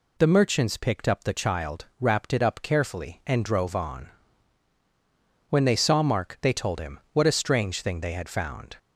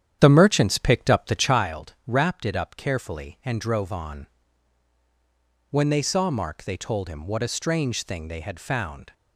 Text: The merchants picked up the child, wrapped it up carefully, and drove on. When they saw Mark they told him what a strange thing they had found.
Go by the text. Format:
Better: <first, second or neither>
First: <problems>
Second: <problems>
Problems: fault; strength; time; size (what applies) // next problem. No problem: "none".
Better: first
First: none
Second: starts louder than the rest; strong; until 1.6 s; 9.5 dB